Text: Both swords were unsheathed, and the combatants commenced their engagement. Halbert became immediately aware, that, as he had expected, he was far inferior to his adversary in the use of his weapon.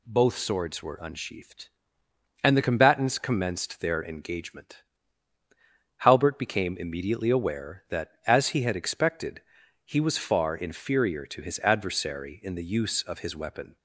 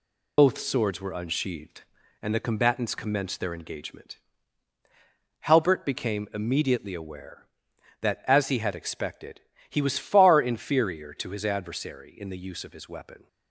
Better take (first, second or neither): first